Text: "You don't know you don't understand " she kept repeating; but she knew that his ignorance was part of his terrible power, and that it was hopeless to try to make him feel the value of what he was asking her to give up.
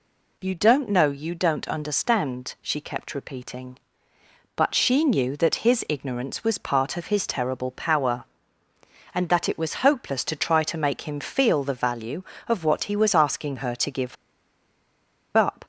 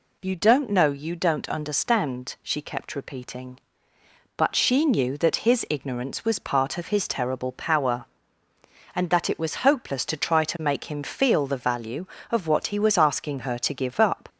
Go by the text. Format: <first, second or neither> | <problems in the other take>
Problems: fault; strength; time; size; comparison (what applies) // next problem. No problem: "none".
second | pauses between "give" and "up"; at 14.1 s; 1.1 s long